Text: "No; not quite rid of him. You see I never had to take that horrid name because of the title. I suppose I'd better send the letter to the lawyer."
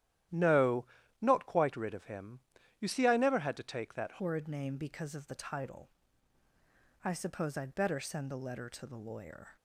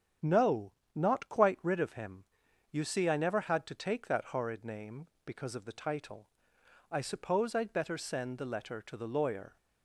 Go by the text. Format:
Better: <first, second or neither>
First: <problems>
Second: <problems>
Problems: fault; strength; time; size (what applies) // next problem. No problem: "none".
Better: second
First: starts louder than the rest; strong; until 1.6 s; 12.5 dB // changes voice at "horrid"; from 4.2 s on; 5.3 s long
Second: starts louder than the rest; strong; until 1.4 s; 8.5 dB